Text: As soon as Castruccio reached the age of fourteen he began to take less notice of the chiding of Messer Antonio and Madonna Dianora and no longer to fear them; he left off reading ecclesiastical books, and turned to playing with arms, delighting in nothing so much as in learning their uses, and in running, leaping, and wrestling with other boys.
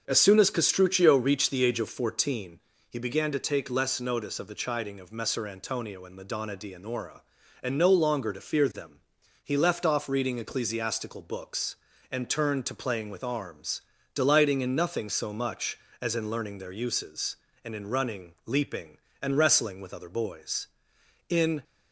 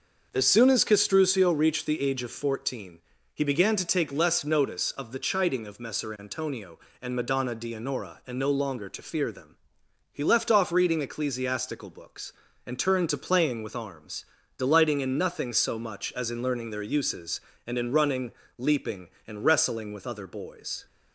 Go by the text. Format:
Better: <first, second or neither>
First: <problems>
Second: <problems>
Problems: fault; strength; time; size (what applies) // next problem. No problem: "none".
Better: second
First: starts louder than the rest; until 1.0 s; 6.5 dB // pauses between "fourteen" and "he"; slight; at 2.5 s; 0.32 s long // goes on to say "In"; slight; from 21.2 s on; 0.36 s long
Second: starts louder than the rest; until 1.3 s; 6.5 dB // pauses between "fourteen" and "he"; slight; at 2.9 s; 0.34 s long